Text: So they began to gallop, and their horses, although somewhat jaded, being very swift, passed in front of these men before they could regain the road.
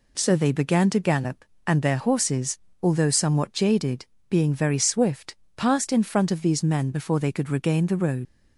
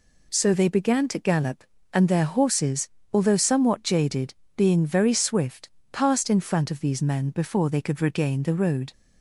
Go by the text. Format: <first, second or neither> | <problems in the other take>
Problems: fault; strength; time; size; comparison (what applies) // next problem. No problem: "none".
second | leaves "road" unfinished; at 8.2 s; 90 ms